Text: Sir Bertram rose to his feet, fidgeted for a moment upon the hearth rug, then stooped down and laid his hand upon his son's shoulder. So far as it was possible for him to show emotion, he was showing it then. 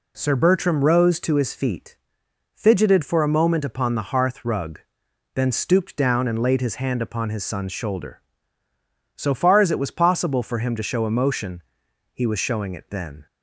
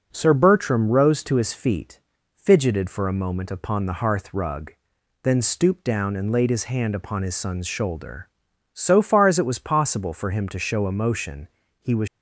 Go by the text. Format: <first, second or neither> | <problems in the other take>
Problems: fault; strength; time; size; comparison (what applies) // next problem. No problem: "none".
first | stops before "showing it then"; at 12.0 s